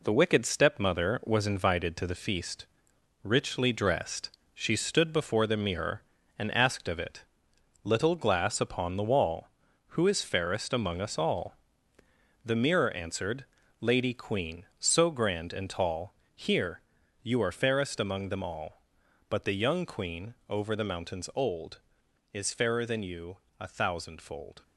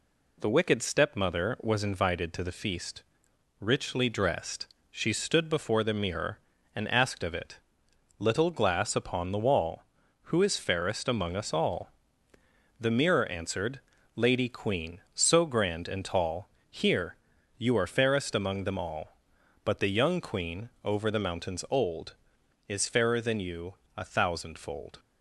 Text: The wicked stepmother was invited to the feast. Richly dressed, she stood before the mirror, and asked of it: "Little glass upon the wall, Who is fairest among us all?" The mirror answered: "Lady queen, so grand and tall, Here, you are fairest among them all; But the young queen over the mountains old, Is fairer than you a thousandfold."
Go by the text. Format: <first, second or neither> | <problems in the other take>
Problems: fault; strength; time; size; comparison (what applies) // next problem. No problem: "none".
second | gets quieter; noticeable; throughout; 6 dB // pauses between "queen" and "over"; slight; at 20.3 s; 0.16 s long; slight in the second // pauses between "you" and "a"; slight; at 23.3 s; 0.24 s long; slight in the second